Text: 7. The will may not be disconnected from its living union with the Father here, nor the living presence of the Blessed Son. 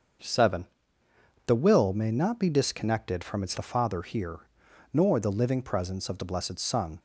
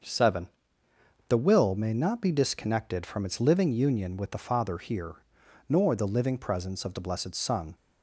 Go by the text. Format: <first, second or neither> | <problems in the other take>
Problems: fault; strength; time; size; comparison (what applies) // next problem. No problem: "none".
second | starts louder than the rest; until 2.0 s; 6.5 dB; also in the second // skips "living union with"; at 3.5 s